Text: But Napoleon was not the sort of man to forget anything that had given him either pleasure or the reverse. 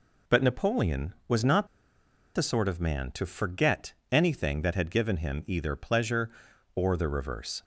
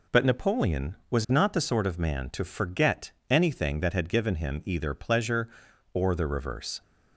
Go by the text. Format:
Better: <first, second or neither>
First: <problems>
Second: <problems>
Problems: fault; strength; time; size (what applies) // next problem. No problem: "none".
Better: second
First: pauses between "not" and "the"; noticeable; at 1.6 s; 0.68 s long // pauses between "forget" and "anything"; slight; at 3.9 s; 0.18 s long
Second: pauses between "forget" and "anything"; slight; at 3.1 s; 0.18 s long